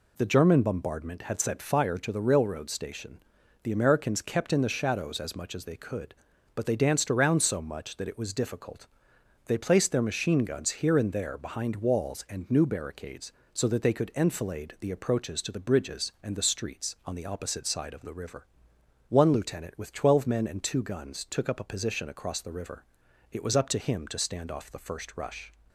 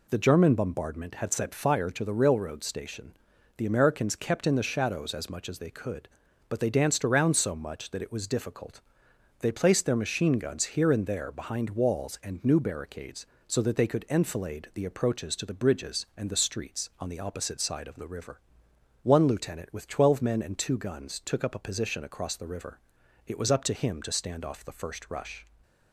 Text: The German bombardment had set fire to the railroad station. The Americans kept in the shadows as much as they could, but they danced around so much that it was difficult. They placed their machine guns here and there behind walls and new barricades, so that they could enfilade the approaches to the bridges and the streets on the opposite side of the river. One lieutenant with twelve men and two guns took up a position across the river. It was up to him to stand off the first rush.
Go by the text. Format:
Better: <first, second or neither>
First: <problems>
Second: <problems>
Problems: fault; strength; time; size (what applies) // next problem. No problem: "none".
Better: neither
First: none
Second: none